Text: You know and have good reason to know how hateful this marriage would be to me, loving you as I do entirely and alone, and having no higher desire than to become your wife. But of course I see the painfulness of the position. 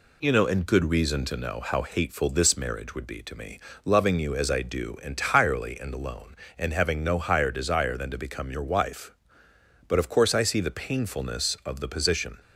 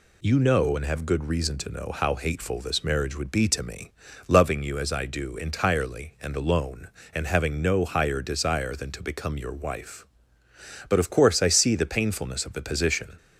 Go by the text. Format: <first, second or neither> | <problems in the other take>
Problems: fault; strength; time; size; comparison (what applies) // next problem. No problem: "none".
second | skips "have"; at 0.6 s